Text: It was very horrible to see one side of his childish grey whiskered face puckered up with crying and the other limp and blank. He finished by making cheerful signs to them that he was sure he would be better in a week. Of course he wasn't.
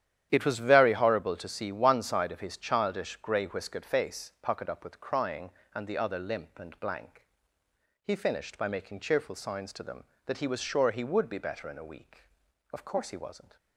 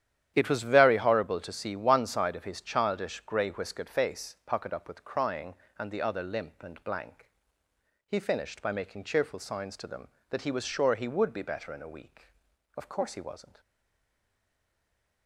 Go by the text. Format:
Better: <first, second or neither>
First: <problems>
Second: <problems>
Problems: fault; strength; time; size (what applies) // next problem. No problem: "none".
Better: first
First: starts louder than the rest; strong; until 1.3 s; 10.5 dB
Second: starts louder than the rest; strong; until 1.3 s; 10.5 dB // stays silent after the last word; noticeable; from 13.5 s on; 1.7 s long